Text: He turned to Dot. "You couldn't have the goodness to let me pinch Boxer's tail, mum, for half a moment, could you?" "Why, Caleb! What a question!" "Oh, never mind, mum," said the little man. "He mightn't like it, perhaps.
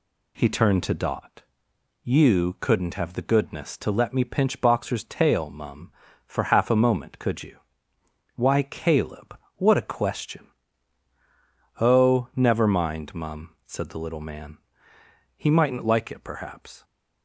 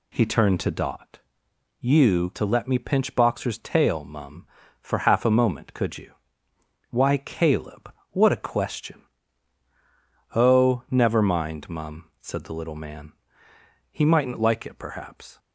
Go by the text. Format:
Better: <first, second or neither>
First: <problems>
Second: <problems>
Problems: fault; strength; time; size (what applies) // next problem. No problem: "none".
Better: first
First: none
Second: skips "couldn't have the goodness"; at 2.3 s